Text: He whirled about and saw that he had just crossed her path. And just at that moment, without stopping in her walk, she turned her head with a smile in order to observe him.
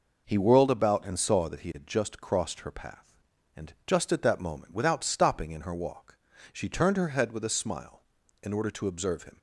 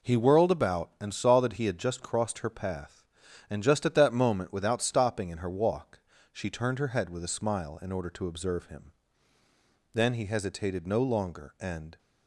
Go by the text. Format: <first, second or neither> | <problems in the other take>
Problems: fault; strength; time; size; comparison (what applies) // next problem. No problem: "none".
first | goes on to say "Then he hesitated no longer and"; strong; from 9.9 s on; 2.0 s long